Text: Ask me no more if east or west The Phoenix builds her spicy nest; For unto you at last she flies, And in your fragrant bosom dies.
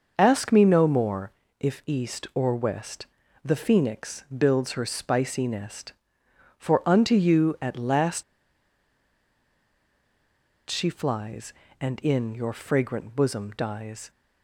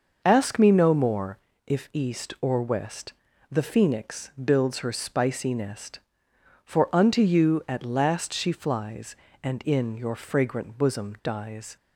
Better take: second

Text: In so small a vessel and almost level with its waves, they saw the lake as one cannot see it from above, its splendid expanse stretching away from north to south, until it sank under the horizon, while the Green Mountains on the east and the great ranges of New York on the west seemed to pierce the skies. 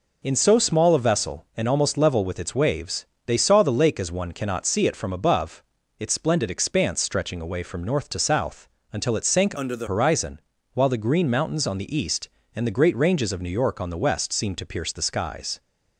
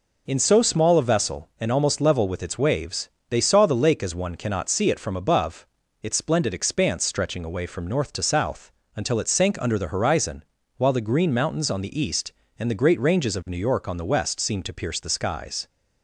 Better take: second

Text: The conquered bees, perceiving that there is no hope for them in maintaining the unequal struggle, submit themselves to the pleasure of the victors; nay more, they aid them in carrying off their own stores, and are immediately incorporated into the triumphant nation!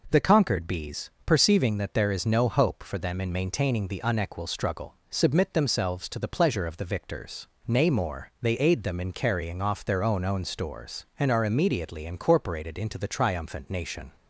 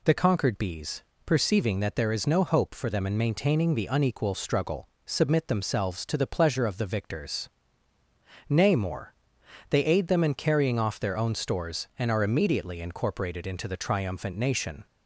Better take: second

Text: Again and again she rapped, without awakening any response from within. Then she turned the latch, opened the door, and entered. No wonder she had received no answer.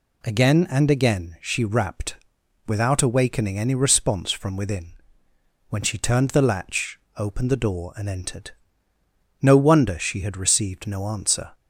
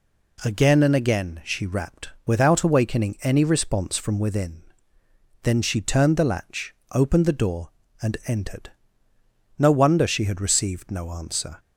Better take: second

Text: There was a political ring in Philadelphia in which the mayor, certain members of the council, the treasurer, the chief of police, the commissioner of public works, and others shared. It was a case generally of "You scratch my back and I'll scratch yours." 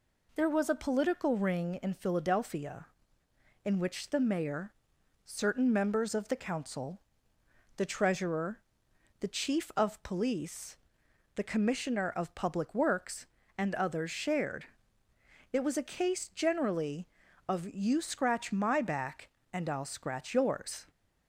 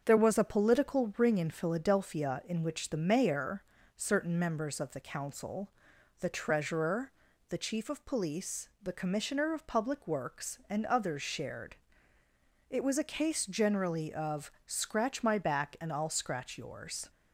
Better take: first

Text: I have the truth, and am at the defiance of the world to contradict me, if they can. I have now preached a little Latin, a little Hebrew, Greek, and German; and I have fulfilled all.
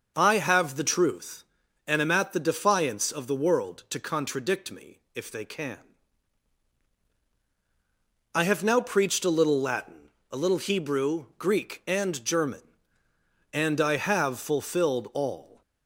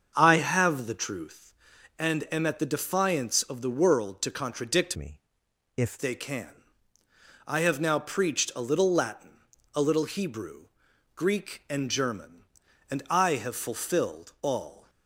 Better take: first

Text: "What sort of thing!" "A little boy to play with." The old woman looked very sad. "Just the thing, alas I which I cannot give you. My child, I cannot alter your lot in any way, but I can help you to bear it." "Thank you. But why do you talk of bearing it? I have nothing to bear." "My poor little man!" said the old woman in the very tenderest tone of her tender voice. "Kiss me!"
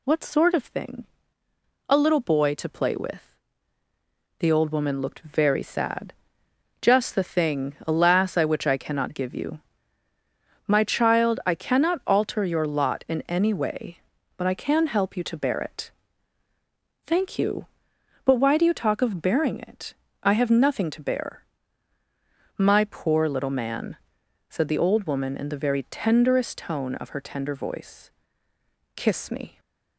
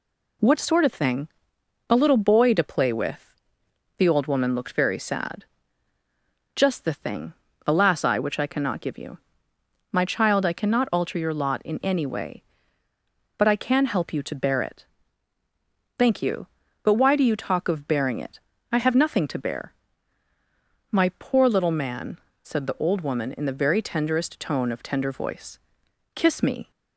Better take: first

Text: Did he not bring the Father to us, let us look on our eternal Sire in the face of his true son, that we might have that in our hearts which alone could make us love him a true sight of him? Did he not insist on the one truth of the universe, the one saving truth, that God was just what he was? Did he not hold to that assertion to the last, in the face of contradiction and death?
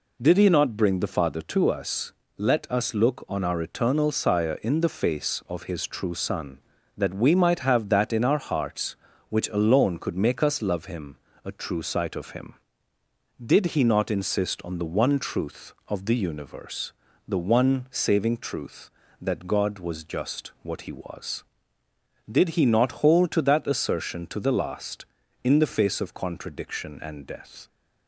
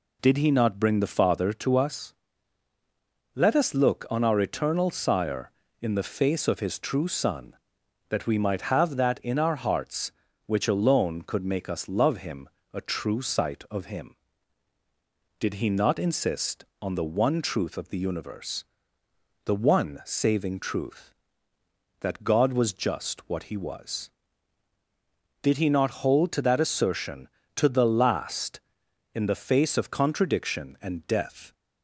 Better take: neither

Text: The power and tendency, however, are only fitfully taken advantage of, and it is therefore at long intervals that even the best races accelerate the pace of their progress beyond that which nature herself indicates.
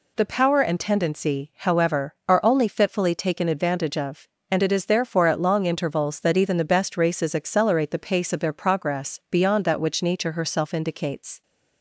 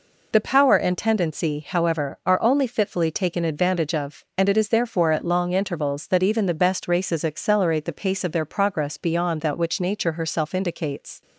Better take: neither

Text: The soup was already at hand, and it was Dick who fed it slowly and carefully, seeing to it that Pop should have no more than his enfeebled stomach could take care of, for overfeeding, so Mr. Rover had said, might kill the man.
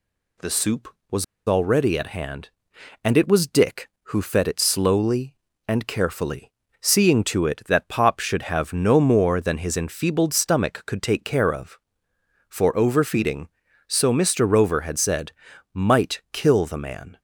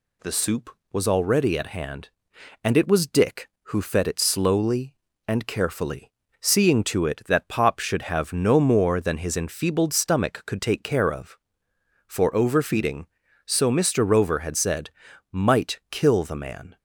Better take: second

